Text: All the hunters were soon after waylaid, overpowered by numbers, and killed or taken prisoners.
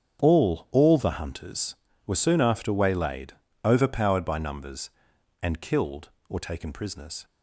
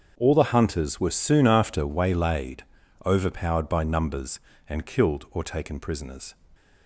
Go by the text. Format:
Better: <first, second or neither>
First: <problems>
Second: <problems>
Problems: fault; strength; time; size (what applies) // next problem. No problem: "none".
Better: second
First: starts louder than the rest; strong; until 1.2 s; 8 dB // says "All" twice; at 0.7 s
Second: starts louder than the rest; strong; until 1.1 s; 7 dB